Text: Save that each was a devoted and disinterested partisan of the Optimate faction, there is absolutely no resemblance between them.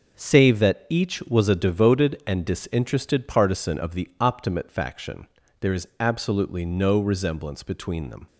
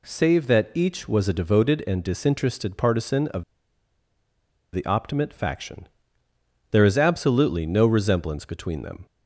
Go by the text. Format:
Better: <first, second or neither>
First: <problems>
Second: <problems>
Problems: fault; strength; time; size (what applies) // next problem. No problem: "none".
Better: first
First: none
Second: pauses between "of" and "the"; strong; at 3.4 s; 1.3 s long